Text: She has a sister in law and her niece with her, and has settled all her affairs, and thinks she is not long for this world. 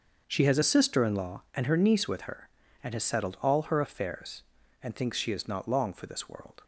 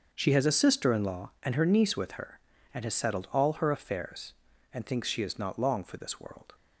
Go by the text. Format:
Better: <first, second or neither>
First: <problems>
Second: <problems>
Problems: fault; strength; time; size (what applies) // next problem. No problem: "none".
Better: neither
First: starts louder than the rest; until 1.2 s; 6.5 dB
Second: starts louder than the rest; noticeable; until 1.1 s; 6 dB